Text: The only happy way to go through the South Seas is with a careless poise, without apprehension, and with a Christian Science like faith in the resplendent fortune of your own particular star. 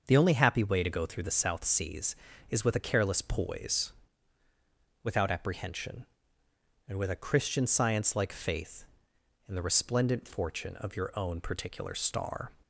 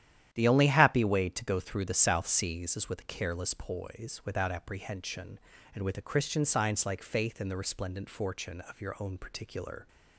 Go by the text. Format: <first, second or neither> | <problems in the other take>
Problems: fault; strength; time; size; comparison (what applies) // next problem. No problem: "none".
first | starts louder than the rest; strong; until 1.3 s; 11 dB; also in the first // stops before "star"; at 9.8 s